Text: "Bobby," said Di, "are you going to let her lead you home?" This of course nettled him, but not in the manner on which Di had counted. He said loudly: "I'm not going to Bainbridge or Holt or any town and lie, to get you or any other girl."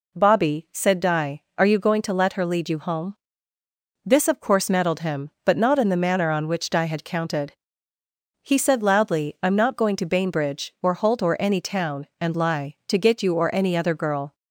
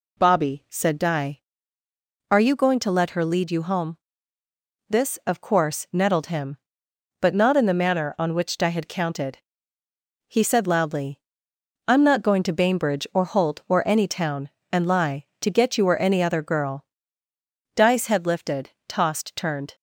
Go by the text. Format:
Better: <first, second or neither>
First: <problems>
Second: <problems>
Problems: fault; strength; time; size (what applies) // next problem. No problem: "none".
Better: first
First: none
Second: goes on to say "Di's head lifted tossed turned"; strong; from 17.7 s on; 2.0 s long